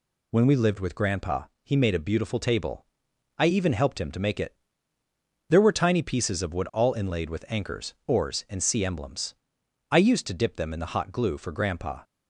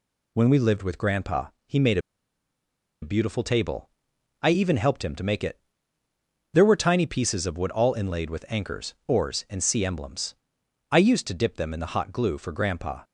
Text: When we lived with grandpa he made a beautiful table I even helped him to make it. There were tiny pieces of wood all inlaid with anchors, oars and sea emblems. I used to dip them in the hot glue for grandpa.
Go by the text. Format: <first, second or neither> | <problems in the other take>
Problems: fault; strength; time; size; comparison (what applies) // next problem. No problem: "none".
first | pauses between "grandpa" and "he"; slight; at 1.4 s; 0.18 s long; slight in the first // pauses between "made" and "a"; at 1.9 s; 1.0 s long // pauses between "table" and "I"; noticeable; at 3.8 s; 0.54 s long; noticeable in the first